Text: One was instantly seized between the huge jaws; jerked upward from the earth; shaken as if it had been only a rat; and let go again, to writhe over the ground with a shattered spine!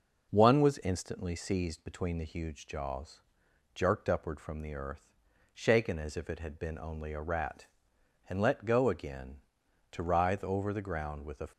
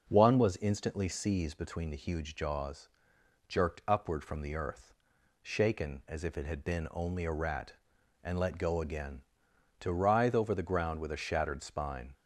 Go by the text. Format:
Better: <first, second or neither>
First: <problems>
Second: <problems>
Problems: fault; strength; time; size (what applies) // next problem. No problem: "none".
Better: second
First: stops before "shattered spine"; at 11.5 s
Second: none